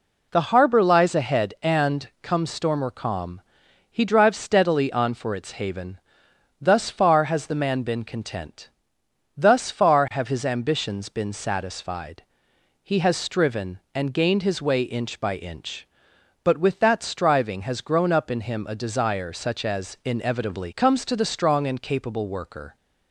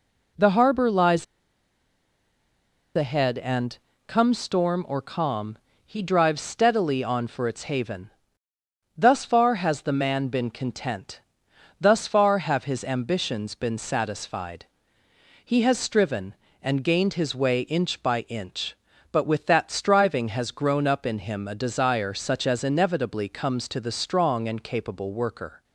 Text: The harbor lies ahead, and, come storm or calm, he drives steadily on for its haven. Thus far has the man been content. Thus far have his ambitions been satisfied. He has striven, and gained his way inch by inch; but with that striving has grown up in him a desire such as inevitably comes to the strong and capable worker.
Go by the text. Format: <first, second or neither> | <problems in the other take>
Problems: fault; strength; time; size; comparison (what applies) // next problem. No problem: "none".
first | pauses between "lies" and "ahead"; strong; at 1.2 s; 1.7 s long